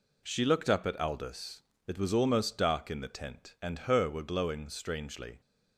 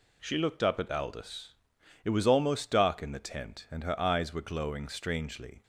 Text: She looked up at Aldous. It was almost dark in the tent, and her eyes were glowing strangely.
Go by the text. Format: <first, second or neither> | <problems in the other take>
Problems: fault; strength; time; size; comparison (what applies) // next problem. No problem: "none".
second | skips "eyes"; at 4.0 s